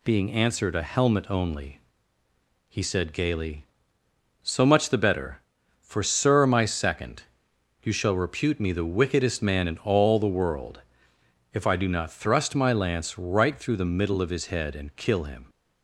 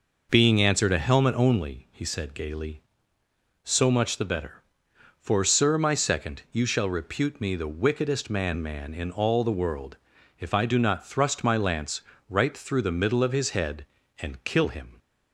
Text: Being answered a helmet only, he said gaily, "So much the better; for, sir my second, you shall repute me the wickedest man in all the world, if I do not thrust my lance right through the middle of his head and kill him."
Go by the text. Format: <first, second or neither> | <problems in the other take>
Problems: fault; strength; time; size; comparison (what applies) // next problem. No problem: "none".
first | says "man" twice; at 8.6 s // pauses between "lance" and "right"; slight; at 12.0 s; 0.26 s long